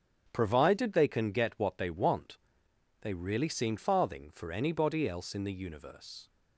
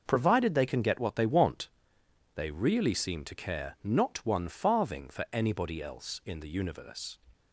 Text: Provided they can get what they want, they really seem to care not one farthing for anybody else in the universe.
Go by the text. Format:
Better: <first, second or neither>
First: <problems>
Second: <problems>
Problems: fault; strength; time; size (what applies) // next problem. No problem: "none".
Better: second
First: starts louder than the rest; strong; until 1.3 s; 7.5 dB // skips "to care not one"; at 3.7 s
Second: none